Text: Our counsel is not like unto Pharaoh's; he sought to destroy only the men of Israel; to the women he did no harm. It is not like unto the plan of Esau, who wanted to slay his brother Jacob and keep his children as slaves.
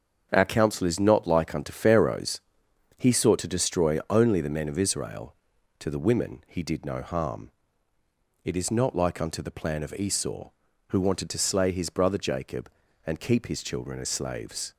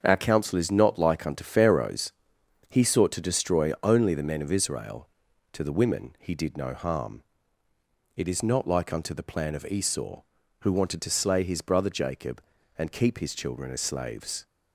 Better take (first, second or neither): neither